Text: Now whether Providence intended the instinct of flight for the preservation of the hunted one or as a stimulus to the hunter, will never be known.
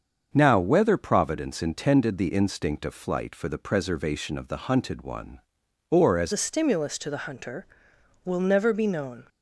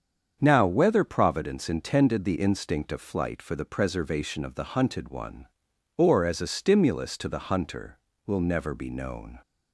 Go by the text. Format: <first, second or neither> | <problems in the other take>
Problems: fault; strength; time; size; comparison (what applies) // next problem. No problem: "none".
second | starts louder than the rest; until 1.3 s; 7 dB; strong in the second // changes voice at "a"; from 6.3 s on; 2.9 s long